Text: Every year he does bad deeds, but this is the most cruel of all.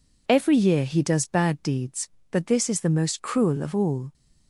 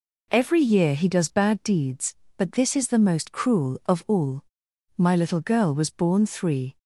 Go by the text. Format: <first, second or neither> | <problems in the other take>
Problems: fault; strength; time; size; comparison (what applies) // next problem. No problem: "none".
first | goes on to say "My little girl was born three"; strong; from 4.9 s on; 1.8 s long